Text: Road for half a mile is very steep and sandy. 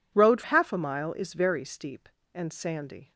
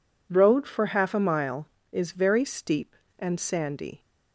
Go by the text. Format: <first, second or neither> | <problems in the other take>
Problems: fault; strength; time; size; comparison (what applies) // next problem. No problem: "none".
second | skips "for"; at 0.4 s